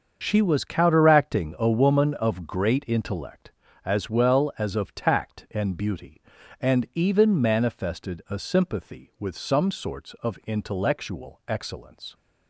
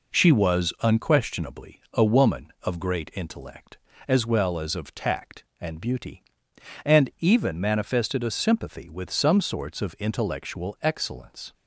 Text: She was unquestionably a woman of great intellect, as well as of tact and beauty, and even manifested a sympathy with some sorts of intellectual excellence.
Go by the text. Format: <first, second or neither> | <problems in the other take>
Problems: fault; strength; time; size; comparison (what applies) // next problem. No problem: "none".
second | starts louder than the rest; until 1.2 s; 7 dB // says "counteracting" for "unquestionably"; at 0.6 s